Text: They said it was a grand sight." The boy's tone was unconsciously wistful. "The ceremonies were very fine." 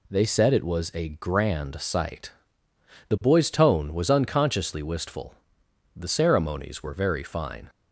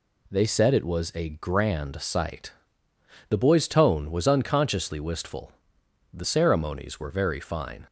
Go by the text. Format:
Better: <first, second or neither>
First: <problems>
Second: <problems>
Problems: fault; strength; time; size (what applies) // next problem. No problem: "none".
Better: neither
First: none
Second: none